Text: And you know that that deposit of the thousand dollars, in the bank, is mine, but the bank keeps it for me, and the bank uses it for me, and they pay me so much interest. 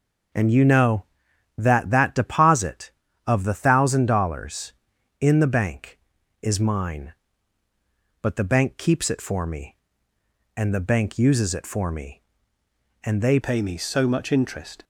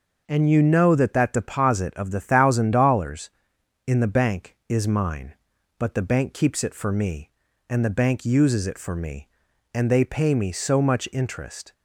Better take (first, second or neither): second